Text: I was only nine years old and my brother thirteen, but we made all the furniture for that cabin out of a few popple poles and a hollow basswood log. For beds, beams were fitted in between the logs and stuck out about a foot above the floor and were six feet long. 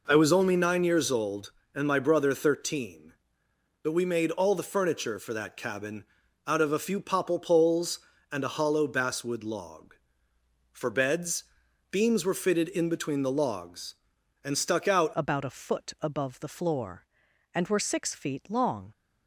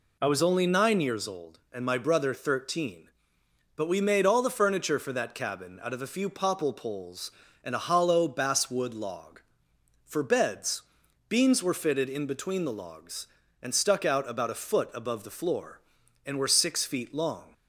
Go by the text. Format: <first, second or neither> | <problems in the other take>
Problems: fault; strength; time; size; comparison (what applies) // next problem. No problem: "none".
second | pauses between "cabin" and "out"; at 6.0 s; 0.42 s long // changes voice at "about"; from 15.1 s on; 3.8 s long